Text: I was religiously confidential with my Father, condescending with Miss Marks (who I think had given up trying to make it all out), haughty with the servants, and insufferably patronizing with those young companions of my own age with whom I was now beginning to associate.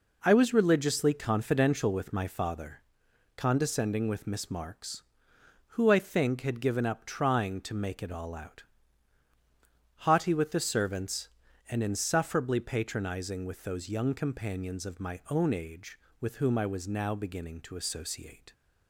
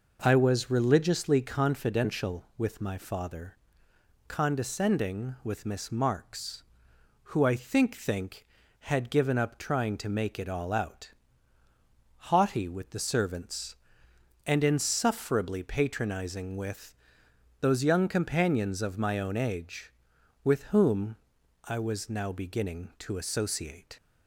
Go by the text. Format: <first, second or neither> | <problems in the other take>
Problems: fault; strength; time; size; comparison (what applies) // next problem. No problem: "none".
first | says "think" twice; at 7.9 s // pauses between "with" and "those"; noticeable; at 16.9 s; 0.66 s long // pauses between "whom" and "I"; noticeable; at 21.1 s; 0.48 s long